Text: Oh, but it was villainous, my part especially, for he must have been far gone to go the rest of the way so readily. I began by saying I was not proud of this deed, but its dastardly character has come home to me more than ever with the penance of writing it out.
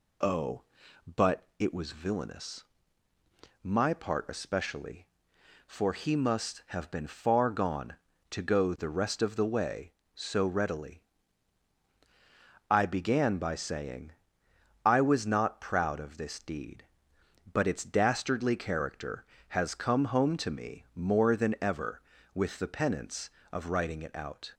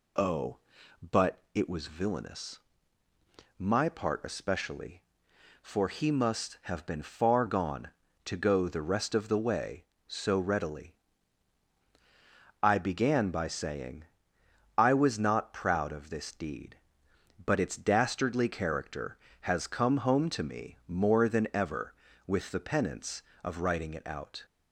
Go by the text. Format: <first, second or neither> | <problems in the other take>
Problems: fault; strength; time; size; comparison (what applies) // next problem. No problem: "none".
neither | pauses between "saying" and "I"; noticeable; the same in both